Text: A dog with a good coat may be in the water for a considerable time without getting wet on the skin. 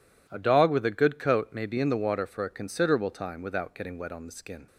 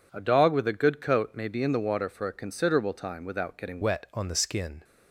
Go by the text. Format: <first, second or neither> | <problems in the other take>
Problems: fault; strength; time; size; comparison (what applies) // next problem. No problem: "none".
first | changes voice at "wet"; from 3.8 s on; 1.0 s long